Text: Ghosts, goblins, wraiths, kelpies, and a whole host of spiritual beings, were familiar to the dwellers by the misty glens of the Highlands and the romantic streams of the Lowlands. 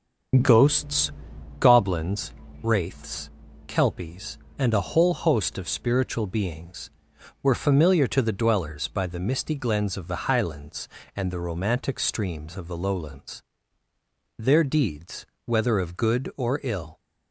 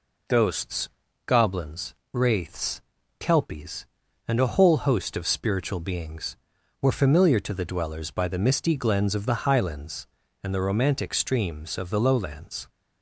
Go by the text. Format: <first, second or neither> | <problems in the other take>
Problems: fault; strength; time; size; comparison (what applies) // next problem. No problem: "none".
second | starts louder than the rest; until 1.9 s; 7 dB // goes on to say "Their deeds whether of good or ill"; strong; from 14.3 s on; 2.6 s long